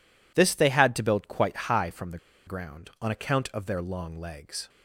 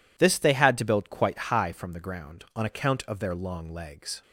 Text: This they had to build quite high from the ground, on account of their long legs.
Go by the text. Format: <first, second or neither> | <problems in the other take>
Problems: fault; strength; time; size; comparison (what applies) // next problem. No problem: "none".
second | pauses between "the" and "ground"; slight; at 2.1 s; 0.27 s long